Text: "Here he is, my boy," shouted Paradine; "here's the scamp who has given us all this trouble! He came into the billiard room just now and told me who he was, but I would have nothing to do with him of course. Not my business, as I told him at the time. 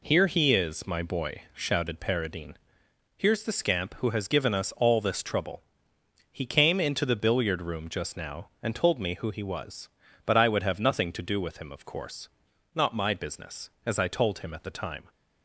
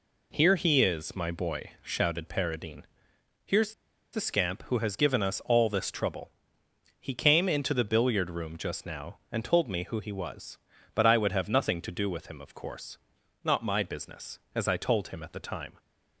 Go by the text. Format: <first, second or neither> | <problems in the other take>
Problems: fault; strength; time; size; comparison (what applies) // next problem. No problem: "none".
first | pauses between "here's" and "the"; at 3.7 s; 0.41 s long